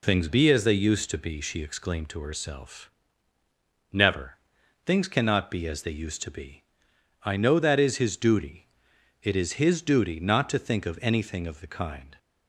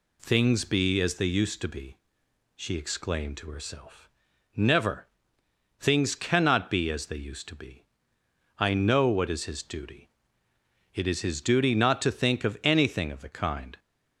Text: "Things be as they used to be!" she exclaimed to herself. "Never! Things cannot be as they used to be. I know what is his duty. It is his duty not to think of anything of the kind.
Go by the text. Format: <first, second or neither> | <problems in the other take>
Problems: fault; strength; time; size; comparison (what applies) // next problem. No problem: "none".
second | says "that" for "what"; at 7.5 s